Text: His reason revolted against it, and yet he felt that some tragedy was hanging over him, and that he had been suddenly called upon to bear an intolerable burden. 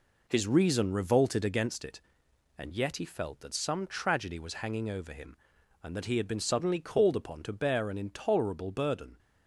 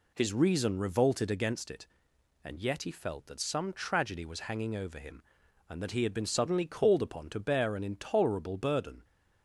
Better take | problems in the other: second | gets quieter; noticeable; throughout; 5.5 dB

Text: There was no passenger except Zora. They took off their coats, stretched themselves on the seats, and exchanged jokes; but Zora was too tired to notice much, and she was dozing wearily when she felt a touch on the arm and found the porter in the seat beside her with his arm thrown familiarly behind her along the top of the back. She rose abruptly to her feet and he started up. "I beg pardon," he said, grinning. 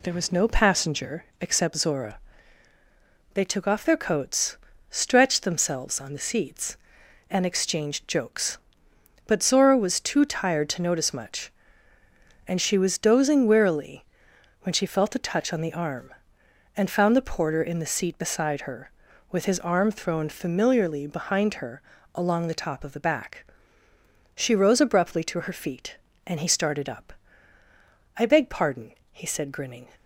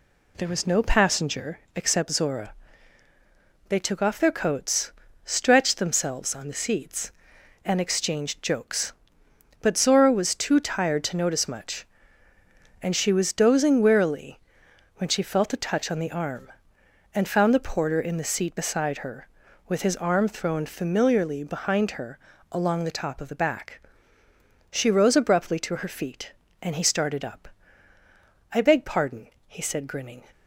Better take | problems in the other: neither | pauses between "wearily" and "when"; noticeable; the same in both // pauses between "her" and "along"; slight; the same in both

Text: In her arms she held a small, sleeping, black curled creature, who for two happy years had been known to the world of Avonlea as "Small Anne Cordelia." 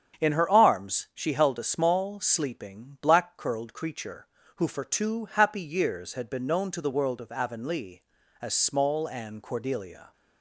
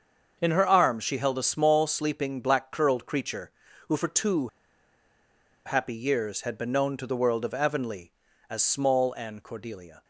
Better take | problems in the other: first | starts louder than the rest; until 1.4 s; 6.5 dB; strong in the first // pauses between "two" and "happy"; at 4.4 s; 1.1 s long

